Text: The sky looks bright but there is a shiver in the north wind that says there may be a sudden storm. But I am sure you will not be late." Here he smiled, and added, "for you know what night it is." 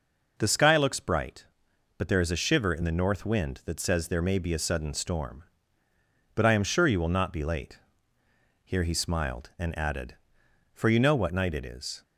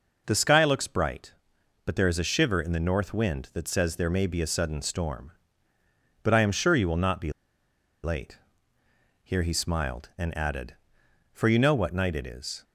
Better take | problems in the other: first | pauses between "be" and "late"; noticeable; at 7.3 s; 0.73 s long

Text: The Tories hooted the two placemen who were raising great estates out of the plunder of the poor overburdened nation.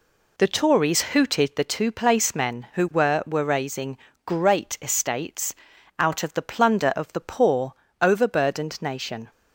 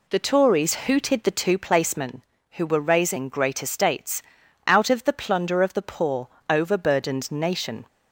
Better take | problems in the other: second | says "were" twice; at 3.2 s // pauses between "raising" and "great"; slight; at 3.9 s; 0.26 s long // pauses between "estates" and "out"; noticeable; at 5.5 s; 0.46 s long; also in the second // pauses between "poor" and "overburdened"; slight; at 7.7 s; 0.26 s long; slight in the second

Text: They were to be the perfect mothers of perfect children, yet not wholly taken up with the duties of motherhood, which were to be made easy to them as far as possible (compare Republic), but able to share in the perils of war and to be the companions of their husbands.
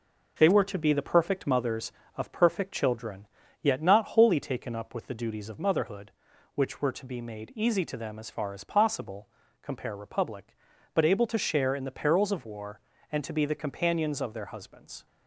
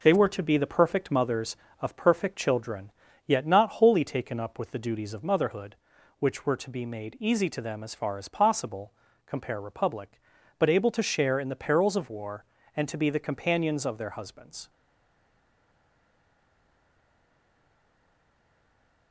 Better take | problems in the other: first | stays silent after the last word; strong; from 14.6 s on; 4.5 s long

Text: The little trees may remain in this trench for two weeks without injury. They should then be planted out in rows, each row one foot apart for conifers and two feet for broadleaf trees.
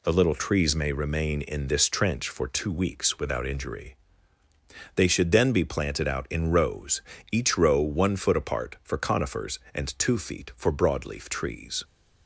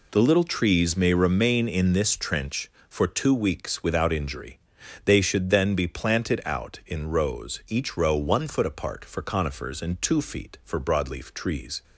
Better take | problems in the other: neither | none

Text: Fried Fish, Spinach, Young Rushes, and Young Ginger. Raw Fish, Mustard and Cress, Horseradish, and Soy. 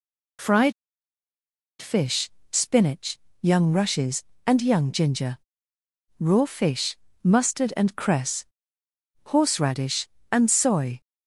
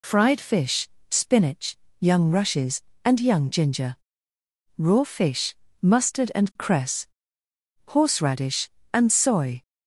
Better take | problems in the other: second | pauses between "Fried" and "Fish"; at 0.7 s; 1.0 s long

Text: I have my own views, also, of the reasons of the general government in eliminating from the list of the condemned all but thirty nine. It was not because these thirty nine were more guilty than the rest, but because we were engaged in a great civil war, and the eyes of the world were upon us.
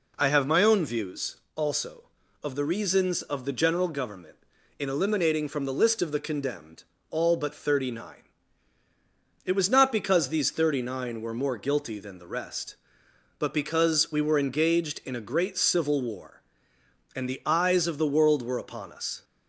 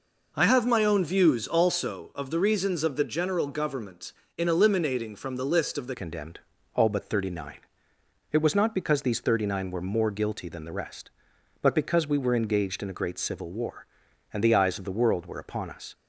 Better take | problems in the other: first | changes voice at "condemned"; from 5.9 s on; 10.0 s long // pauses between "condemned" and "all"; slight; at 6.4 s; 0.34 s long; slight in the first

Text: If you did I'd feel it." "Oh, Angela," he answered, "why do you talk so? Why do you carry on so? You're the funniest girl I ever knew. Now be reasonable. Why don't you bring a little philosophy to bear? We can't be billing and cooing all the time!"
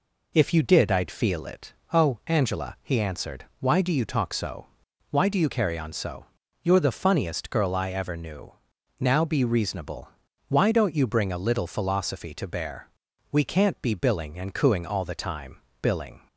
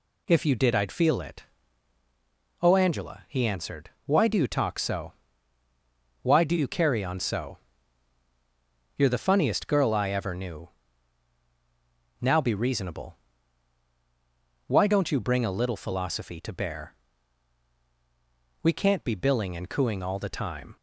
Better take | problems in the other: second | goes on to say "Billing"; slight; from 15.8 s on; 0.46 s long

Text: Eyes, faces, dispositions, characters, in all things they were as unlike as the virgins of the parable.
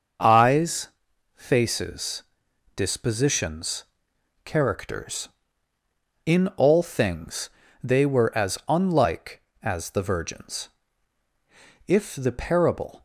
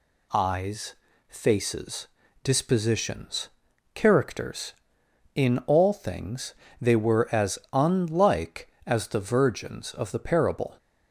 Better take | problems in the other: second | starts louder than the rest; noticeable; until 1.6 s; 6 dB // pauses between "things" and "they"; slight; at 7.4 s; 0.34 s long; slight in the second // says "if" for "of"; at 11.8 s

